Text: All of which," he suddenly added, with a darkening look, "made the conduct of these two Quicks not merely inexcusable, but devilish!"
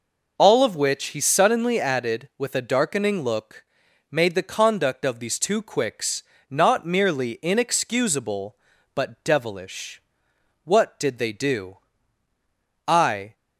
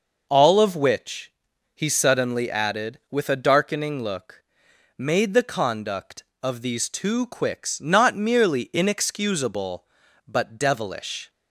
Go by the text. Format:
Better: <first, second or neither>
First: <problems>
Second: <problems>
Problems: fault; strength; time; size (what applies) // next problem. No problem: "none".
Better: second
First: pauses between "Quicks" and "not"; slight; at 6.2 s; 0.26 s long // goes on to say "What did they do I"; strong; from 10.6 s on; 2.7 s long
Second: none